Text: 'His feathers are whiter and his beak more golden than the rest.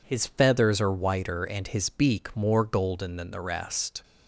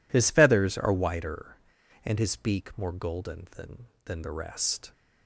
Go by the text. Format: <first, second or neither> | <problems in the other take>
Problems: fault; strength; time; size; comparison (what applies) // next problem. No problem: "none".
first | says "than" twice; at 4.0 s